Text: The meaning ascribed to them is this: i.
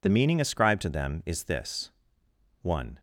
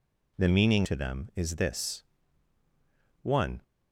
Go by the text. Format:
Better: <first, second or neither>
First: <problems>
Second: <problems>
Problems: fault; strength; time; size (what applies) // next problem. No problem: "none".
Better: first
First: none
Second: skips "ascribed"; at 0.8 s